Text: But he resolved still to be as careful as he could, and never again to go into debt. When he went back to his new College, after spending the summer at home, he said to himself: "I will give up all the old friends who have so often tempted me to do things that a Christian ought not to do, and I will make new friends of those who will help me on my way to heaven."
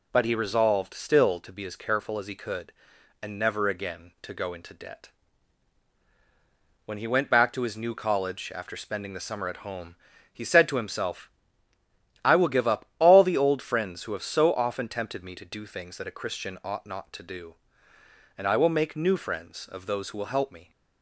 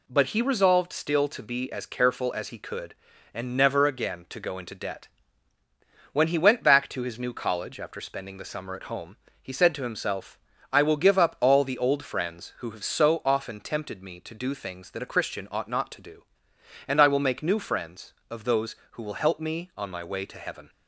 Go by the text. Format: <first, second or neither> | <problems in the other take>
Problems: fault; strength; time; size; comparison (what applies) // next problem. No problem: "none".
second | stops before "on my way to heaven"; at 20.7 s